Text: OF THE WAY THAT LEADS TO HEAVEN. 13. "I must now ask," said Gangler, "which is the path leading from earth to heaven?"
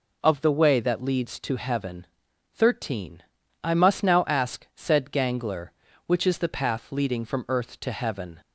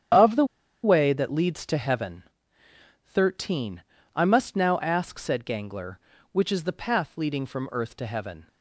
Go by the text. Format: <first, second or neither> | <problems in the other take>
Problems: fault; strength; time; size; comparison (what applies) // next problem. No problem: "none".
first | starts louder than the rest; strong; until 1.5 s; 9 dB // pauses between "THE" and "WAY"; at 0.4 s; 0.38 s long